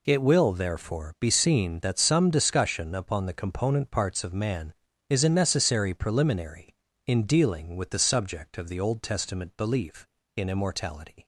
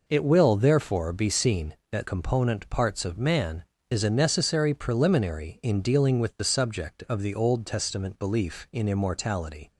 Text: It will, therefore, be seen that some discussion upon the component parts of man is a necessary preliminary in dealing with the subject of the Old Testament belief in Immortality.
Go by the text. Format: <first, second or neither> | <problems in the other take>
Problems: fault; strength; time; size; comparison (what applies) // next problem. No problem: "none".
first | skips "some discussion upon the"; at 2.0 s